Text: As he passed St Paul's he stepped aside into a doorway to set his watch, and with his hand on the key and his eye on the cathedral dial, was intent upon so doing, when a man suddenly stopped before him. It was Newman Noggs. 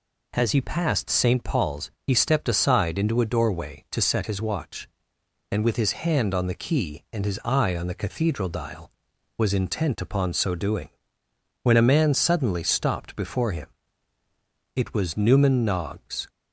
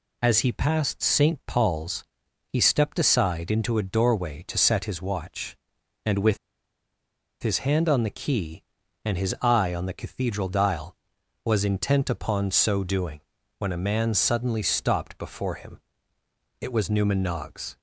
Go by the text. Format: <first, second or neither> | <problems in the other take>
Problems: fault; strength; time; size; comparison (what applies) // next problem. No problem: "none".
first | pauses between "Paul's" and "he"; at 2.0 s; 0.44 s long; slight in the first // pauses between "with" and "his"; at 6.3 s; 1.0 s long